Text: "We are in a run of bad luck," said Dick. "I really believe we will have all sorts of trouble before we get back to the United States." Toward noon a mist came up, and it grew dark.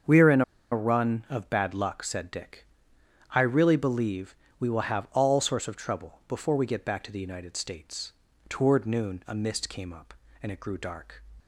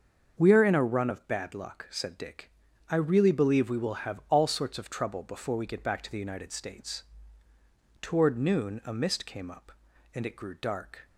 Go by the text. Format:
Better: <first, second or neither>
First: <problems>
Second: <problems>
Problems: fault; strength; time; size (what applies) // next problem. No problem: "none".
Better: second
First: starts louder than the rest; until 1.4 s; 7 dB // pauses between "in" and "a"; slight; at 0.4 s; 0.29 s long // pauses between "believe" and "we"; slight; at 4.3 s; 0.28 s long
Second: starts louder than the rest; until 1.4 s; 6.5 dB